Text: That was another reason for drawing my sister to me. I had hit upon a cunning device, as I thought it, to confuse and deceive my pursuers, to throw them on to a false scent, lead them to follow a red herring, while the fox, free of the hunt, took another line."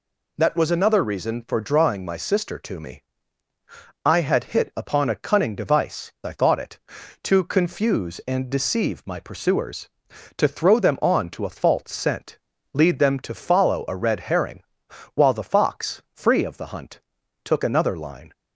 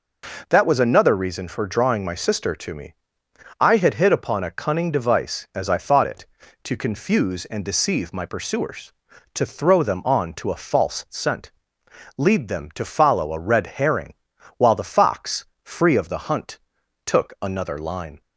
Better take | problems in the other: second | skips "as"; at 6.1 s

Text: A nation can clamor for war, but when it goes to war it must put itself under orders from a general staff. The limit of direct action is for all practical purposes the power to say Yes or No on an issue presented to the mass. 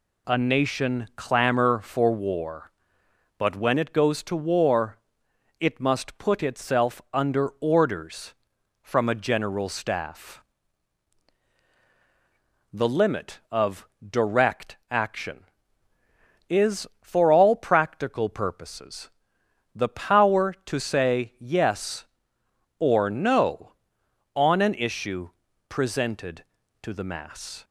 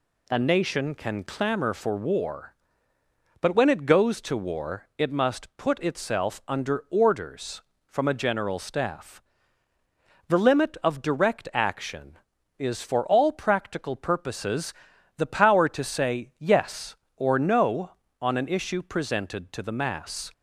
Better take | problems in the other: second | skips "can"; at 1.1 s // pauses between "war" and "it"; noticeable; at 4.9 s; 0.62 s long // pauses between "of" and "direct"; slight; at 13.8 s; 0.20 s long // pauses between "purposes" and "the"; noticeable; at 19.0 s; 0.66 s long; also in the second // pauses between "issue" and "presented"; at 25.2 s; 0.38 s long

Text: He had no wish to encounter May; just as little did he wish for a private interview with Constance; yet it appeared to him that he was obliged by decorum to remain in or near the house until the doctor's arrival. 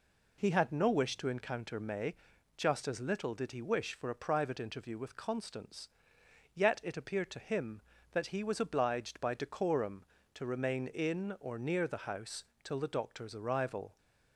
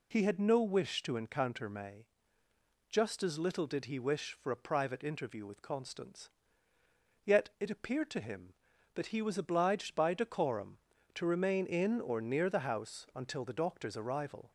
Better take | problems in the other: second | says "till" for "until"; at 12.6 s

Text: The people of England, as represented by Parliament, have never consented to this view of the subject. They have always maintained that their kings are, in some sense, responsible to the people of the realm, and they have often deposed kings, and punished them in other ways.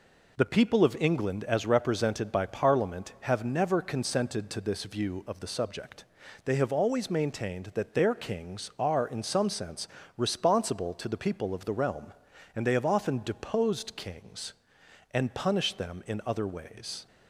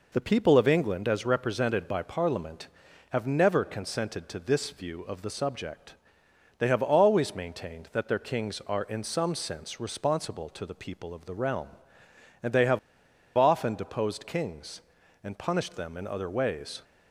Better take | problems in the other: first | pauses between "have" and "often"; noticeable; at 12.7 s; 0.56 s long

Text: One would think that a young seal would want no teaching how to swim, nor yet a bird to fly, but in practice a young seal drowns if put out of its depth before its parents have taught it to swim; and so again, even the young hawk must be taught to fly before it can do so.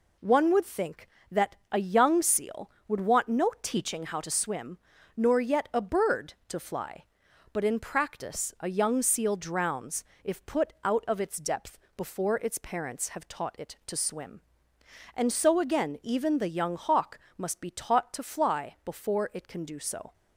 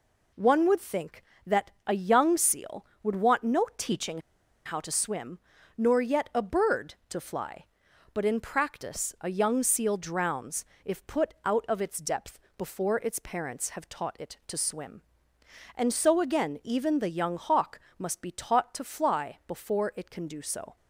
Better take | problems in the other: first | pauses between "teaching" and "how"; at 4.2 s; 0.44 s long // pauses between "drowns" and "if"; slight; at 10.6 s; 0.20 s long; slight in the first // pauses between "depth" and "before"; slight; at 12.3 s; 0.20 s long; slight in the first // pauses between "hawk" and "must"; slight; at 17.7 s; 0.18 s long; slight in the first

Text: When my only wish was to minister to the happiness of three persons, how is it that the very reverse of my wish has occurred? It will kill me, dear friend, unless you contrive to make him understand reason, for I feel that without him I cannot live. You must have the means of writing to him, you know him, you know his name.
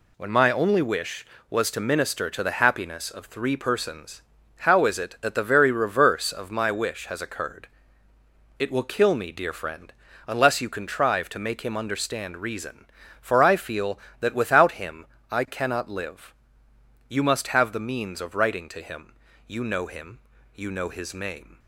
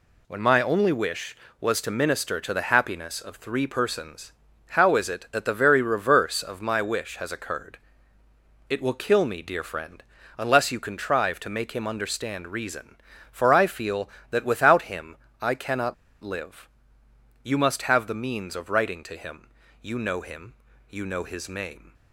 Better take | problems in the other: first | pauses between "him" and "I"; slight; at 15.1 s; 0.28 s long; slight in the first // pauses between "cannot" and "live"; slight; at 15.9 s; 0.28 s long

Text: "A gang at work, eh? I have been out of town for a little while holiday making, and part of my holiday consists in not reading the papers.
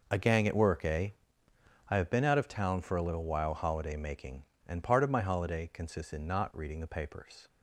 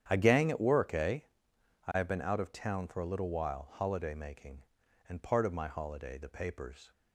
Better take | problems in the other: first | starts louder than the rest; strong; until 1.0 s; 9.5 dB // skips "consists in not reading"; at 6.1 s

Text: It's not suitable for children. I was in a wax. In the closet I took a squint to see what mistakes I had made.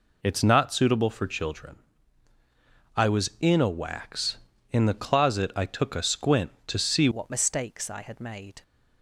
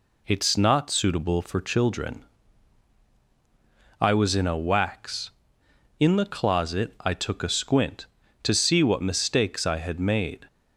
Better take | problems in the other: second | changes voice at "what"; from 7.1 s on; 1.5 s long

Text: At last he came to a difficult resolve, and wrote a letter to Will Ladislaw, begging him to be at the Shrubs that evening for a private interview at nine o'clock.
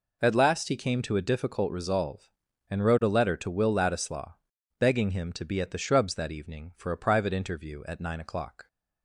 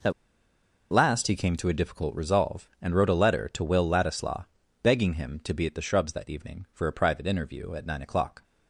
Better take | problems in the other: first | pauses between "At" and "last"; noticeable; at 0.1 s; 0.80 s long

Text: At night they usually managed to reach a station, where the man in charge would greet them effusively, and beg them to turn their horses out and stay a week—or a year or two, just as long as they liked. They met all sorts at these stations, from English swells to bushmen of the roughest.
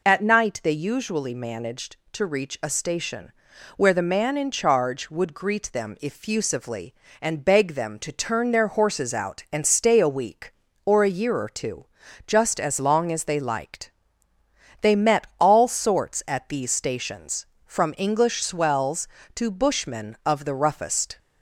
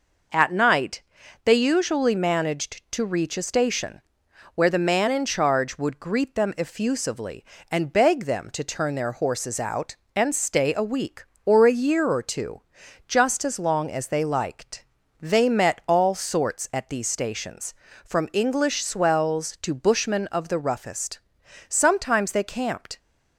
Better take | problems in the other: first | pauses between "night" and "they"; at 1.0 s; 0.42 s long // goes on to say "Sometimes they camped"; noticeable; from 21.6 s on; 1.3 s long

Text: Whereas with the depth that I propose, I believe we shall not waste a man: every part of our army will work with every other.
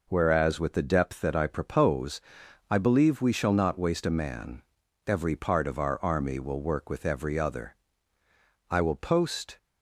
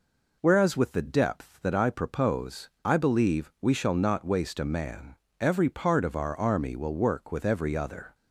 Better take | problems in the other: second | goes on to say "I will post"; noticeable; from 8.6 s on; 0.88 s long

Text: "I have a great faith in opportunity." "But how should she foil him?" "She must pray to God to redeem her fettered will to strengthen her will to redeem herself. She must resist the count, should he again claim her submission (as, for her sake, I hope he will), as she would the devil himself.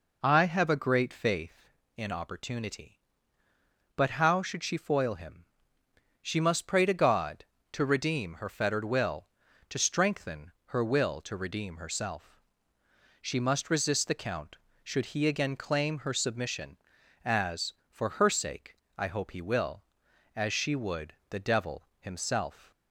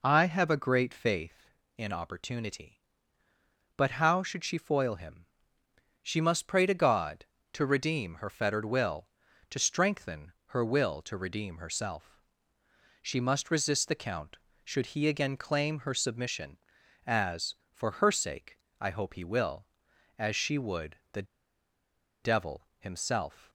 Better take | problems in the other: first | pauses between "would" and "the"; slight; at 20.9 s; 0.16 s long; slight in the first // pauses between "the" and "devil"; at 21.2 s; 0.99 s long

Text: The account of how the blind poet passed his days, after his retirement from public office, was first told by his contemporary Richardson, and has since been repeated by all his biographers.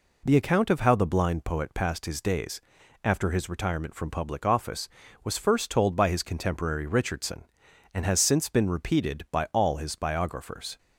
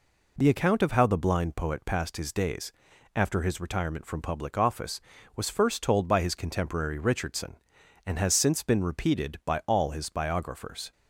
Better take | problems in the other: neither | none

